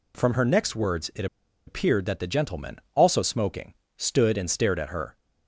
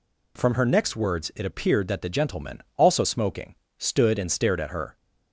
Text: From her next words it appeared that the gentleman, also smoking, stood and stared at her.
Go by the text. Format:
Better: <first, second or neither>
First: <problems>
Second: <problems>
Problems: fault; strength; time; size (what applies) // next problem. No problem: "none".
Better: second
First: pauses between "it" and "appeared"; at 1.2 s; 0.41 s long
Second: none